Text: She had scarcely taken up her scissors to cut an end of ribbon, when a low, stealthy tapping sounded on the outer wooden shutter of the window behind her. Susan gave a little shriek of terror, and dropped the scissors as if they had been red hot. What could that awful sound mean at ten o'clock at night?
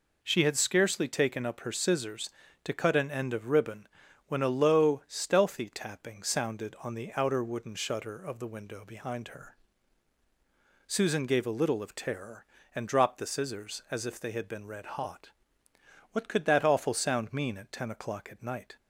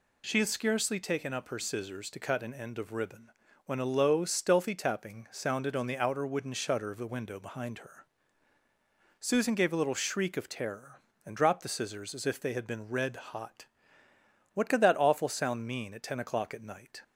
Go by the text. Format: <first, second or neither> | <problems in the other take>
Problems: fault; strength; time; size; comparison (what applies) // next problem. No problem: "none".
second | skips "shriek"; at 11.8 s